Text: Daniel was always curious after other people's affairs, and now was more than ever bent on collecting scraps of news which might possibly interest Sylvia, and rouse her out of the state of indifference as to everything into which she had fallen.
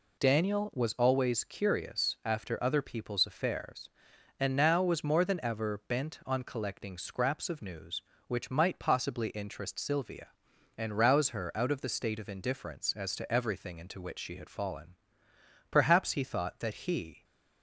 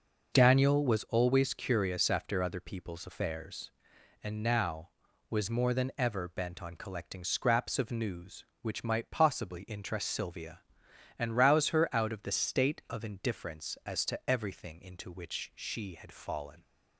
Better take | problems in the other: second | goes on to say "Perhaps he thought that he"; from 15.6 s on; 1.5 s long

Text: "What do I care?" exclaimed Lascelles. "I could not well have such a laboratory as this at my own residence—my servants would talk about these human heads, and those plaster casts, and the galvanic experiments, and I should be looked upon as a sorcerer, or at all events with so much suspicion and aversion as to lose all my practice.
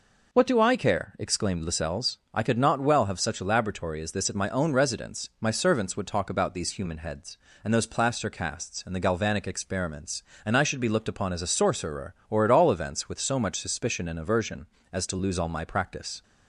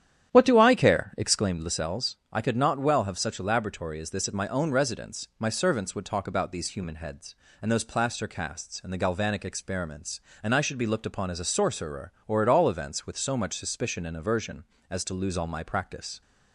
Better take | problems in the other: first | starts louder than the rest; strong; until 1.6 s; 10 dB

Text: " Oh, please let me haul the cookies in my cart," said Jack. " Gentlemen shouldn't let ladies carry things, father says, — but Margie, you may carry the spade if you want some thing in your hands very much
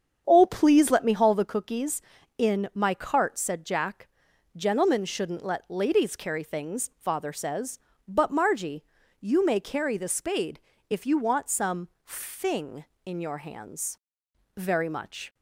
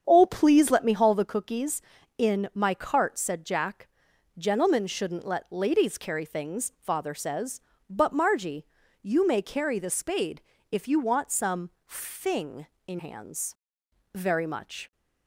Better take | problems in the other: first | starts louder than the rest; strong; until 1.0 s; 7.5 dB; strong in the first // pauses between "spade" and "if"; slight; at 10.4 s; 0.28 s long; slight in the first // pauses between "some" and "thing"; slight; at 11.7 s; 0.16 s long; slight in the first // skips "your"; at 12.9 s // pauses between "hands" and "very"; noticeable; at 13.5 s; 0.58 s long; noticeable in the first

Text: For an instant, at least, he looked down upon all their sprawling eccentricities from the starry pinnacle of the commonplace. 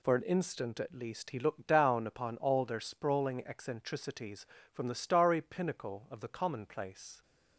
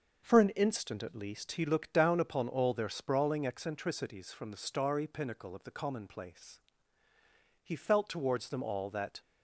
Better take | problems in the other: first | starts louder than the rest; noticeable; until 1.2 s; 6 dB // goes on to say "He felt towards them all that"; from 7.6 s on; 1.5 s long

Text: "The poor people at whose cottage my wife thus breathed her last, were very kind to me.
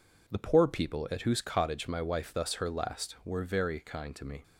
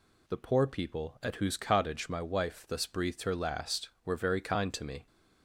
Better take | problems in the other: second | skips "breathed"; at 2.5 s

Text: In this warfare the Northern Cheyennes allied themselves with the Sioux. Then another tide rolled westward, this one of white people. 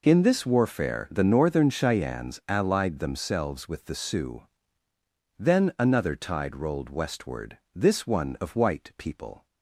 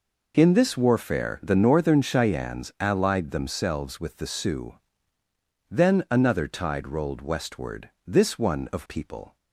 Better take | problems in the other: first | skips "white"; at 8.8 s

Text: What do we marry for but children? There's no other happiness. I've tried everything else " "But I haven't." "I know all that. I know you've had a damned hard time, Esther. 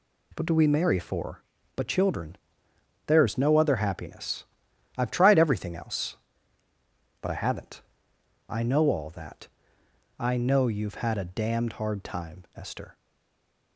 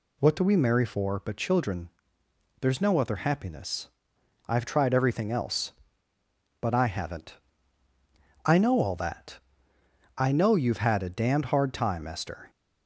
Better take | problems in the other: second | stays silent after the last word; slight; from 12.9 s on; 0.8 s long

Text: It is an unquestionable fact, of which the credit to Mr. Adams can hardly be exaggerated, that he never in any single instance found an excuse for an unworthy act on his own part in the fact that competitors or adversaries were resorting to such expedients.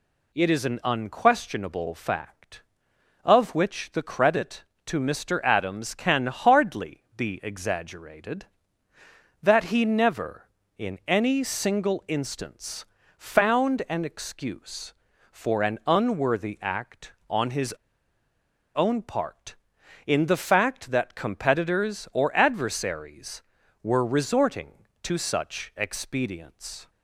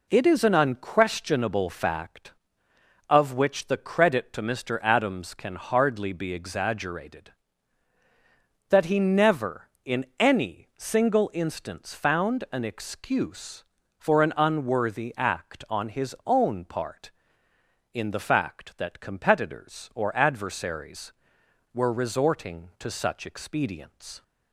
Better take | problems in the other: second | pauses between "hardly" and "be"; slight; at 7.0 s; 0.16 s long // pauses between "instance" and "found"; slight; at 12.8 s; 0.32 s long // pauses between "his" and "own"; at 17.7 s; 1.0 s long

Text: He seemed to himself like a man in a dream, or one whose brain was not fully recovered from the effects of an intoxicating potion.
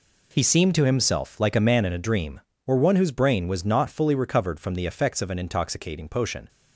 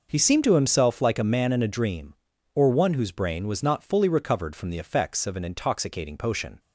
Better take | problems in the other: neither | none

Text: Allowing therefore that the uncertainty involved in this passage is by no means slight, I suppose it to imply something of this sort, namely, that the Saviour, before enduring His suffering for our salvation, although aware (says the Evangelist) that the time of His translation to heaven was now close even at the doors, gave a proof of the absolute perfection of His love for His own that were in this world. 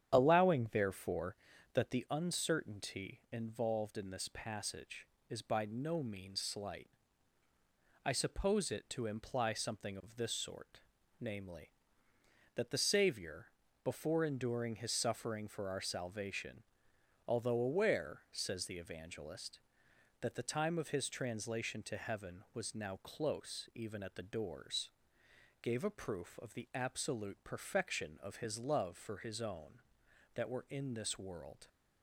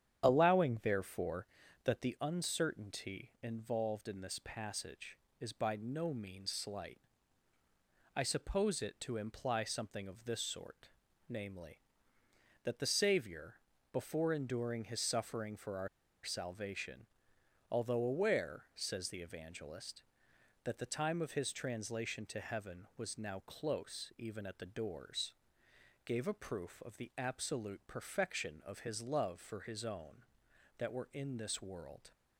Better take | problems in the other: first | starts louder than the rest; strong; until 1.2 s; 9 dB; strong in the first // pauses between "our" and "salvation"; at 15.8 s; 0.36 s long

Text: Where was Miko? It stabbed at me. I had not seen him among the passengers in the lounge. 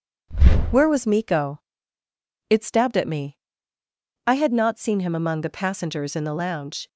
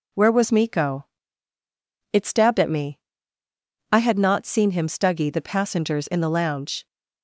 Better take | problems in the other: first | says "stuggy" for "among"; at 4.8 s

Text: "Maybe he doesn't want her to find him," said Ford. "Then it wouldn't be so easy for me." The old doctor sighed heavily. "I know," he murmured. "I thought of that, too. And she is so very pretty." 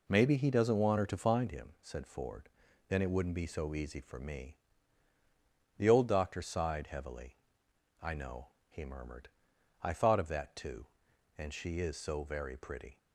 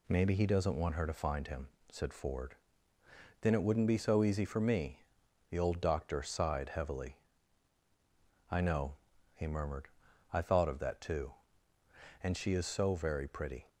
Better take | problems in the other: neither | none

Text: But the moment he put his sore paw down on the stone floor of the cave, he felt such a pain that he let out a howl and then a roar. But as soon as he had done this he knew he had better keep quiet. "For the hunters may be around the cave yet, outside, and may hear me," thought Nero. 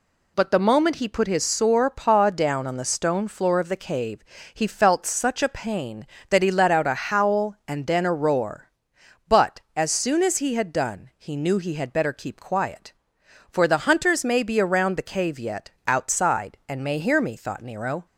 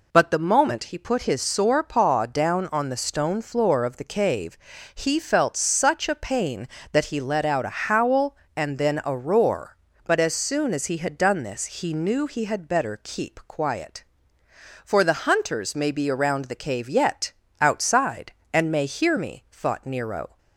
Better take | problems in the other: second | skips "this"; at 11.1 s

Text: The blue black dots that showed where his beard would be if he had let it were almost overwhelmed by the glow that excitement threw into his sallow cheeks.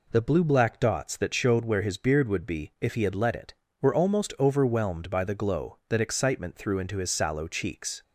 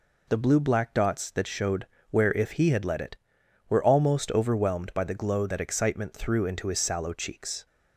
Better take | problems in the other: first | pauses between "showed" and "where"; slight; at 1.8 s; 0.22 s long // skips "his beard would be"; at 2.3 s

